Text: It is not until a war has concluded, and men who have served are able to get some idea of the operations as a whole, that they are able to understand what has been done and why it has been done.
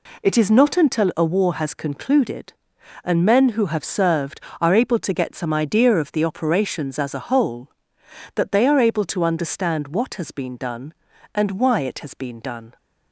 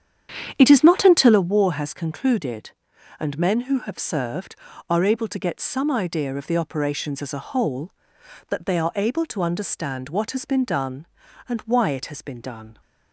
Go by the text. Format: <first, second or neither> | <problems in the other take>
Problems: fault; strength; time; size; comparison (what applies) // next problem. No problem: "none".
first | starts louder than the rest; strong; until 1.4 s; 9 dB